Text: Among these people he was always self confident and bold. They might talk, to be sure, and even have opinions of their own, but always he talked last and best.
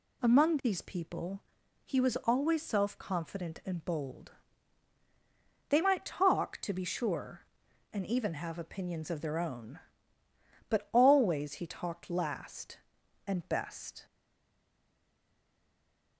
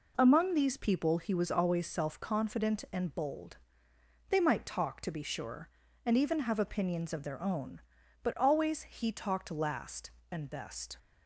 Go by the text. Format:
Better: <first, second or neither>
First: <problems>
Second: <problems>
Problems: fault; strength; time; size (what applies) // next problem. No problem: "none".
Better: second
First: pauses between "people" and "he"; at 1.4 s; 0.44 s long // stays silent after the last word; from 14.0 s on; 2.1 s long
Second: none